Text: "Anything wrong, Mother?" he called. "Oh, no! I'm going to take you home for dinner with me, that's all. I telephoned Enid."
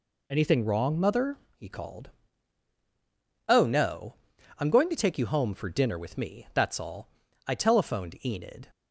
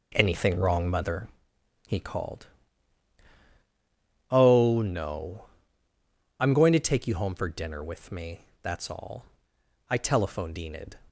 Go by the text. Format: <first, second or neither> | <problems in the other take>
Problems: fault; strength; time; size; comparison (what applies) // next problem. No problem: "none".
first | starts louder than the rest; noticeable; until 1.3 s; 4 dB